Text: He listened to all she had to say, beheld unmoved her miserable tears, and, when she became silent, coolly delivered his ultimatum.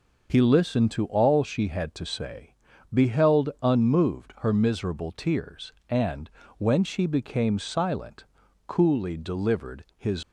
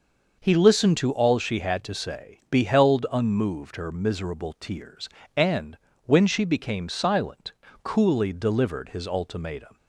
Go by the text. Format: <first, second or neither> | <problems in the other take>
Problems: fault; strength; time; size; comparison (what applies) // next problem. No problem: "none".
second | stops before "ultimatum"; at 10.2 s